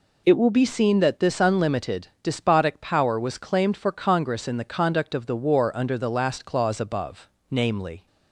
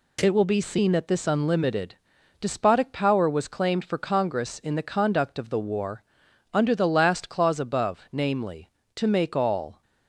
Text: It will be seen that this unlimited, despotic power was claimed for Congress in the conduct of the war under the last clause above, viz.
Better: first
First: none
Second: pauses between "war" and "under"; noticeable; at 6.0 s; 0.48 s long // goes on to say "to make all"; noticeable; from 8.9 s on; 0.86 s long

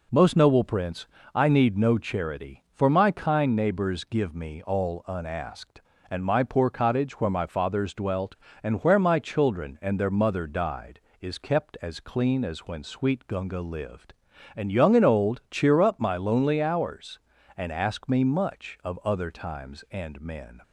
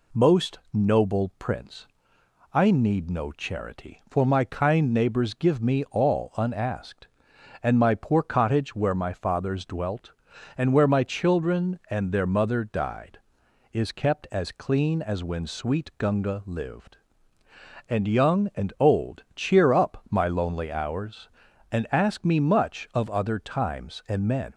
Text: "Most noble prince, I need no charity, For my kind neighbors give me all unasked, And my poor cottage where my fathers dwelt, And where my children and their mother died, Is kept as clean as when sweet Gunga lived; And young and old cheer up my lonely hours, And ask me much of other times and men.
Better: neither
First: none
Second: none

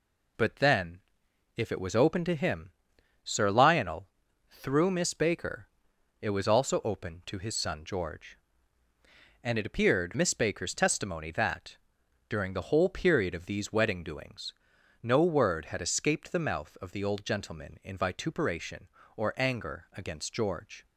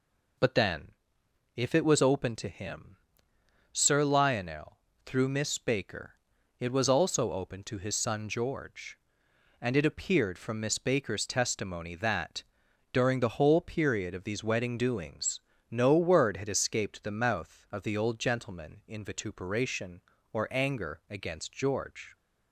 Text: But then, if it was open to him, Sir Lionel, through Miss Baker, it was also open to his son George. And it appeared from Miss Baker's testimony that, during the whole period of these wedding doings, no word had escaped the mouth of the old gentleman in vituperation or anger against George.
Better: second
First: skips "from"; at 10.1 s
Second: none

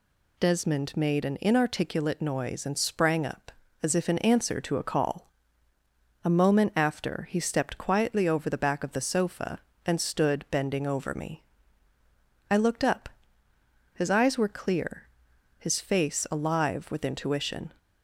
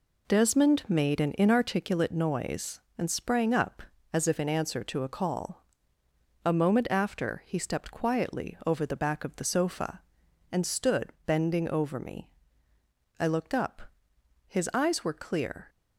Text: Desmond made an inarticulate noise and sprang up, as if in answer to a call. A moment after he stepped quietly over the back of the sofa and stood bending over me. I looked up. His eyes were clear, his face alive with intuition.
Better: first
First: none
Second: pauses between "stood" and "bending"; slight; at 11.1 s; 0.16 s long // stops before "his face alive with intuition"; at 15.6 s

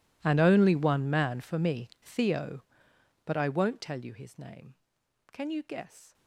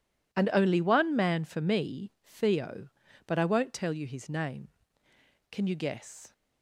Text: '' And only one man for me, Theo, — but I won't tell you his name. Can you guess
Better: second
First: gets quieter; strong; throughout; 22 dB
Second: none

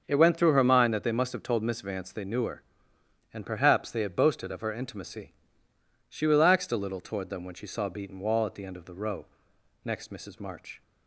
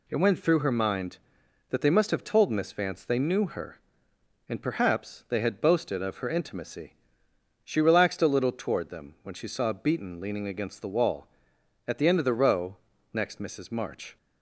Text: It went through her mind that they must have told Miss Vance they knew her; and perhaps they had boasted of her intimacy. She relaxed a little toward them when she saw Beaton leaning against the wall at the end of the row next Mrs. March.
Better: second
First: starts louder than the rest; until 1.0 s; 6.5 dB // skips "leaning against the"; at 8.1 s // pauses between "row" and "next"; noticeable; at 9.2 s; 0.60 s long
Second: pauses between "row" and "next"; slight; at 12.7 s; 0.36 s long

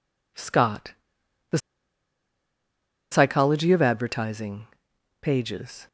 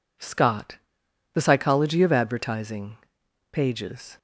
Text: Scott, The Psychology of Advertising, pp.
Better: second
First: pauses between "The" and "Psychology"; strong; at 1.5 s; 1.5 s long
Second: none

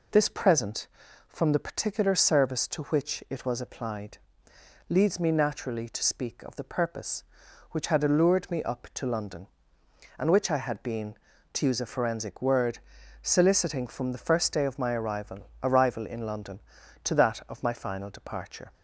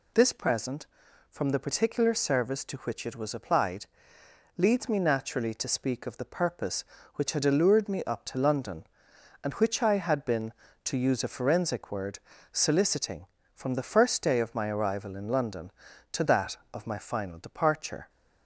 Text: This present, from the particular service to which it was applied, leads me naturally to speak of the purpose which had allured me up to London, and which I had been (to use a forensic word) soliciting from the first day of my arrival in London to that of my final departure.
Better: second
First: says "arrival" twice; at 15.6 s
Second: none

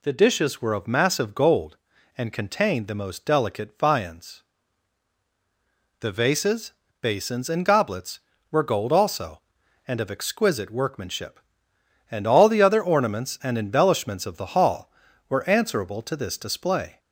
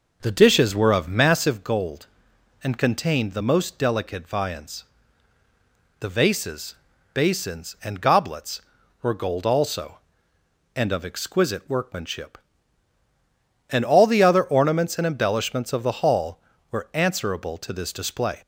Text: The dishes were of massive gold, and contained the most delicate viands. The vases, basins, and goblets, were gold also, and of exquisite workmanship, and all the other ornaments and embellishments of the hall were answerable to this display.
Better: first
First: none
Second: starts louder than the rest; noticeable; until 1.7 s; 5.5 dB

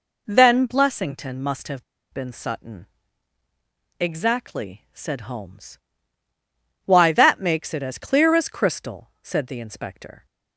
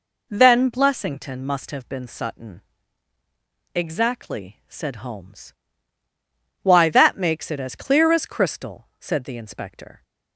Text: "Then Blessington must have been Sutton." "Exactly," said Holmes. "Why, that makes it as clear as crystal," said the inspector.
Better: second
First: pauses between "have" and "been"; slight; at 1.8 s; 0.29 s long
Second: none

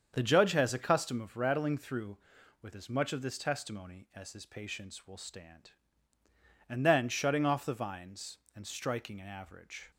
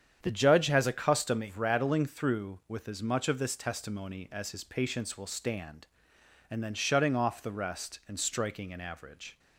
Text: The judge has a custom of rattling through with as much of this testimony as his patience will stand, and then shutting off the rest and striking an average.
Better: second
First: starts louder than the rest; strong; until 1.1 s; 7 dB // says "vines" for "rest"; at 7.7 s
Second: starts louder than the rest; strong; until 1.2 s; 8.5 dB

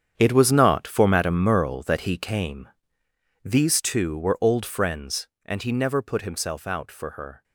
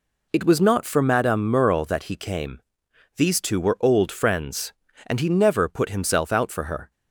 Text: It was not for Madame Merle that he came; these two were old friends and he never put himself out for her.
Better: second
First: gets quieter; strong; throughout; 13.5 dB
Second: none

